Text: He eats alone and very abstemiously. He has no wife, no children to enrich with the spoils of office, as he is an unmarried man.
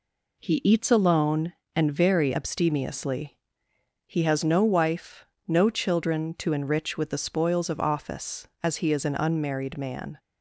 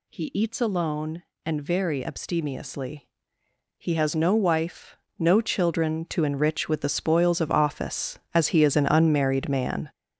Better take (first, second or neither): first